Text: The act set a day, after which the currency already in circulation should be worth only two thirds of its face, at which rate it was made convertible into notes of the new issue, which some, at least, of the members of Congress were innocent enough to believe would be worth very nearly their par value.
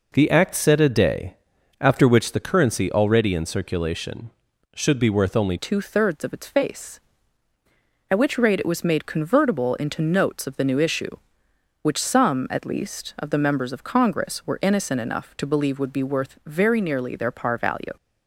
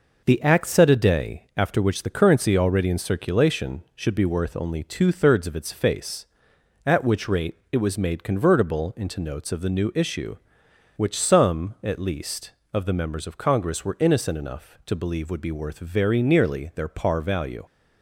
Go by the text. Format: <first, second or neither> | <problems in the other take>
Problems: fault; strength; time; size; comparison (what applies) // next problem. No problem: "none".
second | changes voice at "two"; from 5.5 s on; 12.4 s long